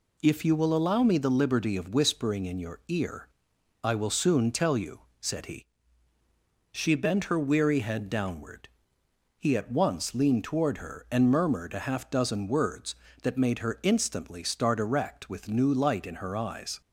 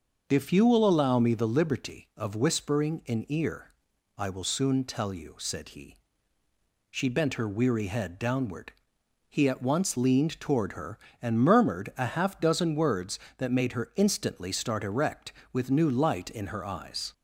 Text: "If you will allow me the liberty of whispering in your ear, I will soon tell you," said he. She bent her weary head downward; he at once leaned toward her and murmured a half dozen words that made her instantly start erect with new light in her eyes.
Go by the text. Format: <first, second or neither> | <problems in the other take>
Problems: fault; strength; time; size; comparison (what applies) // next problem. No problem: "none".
first | starts louder than the rest; until 1.2 s; 6 dB // skips "your"; at 3.2 s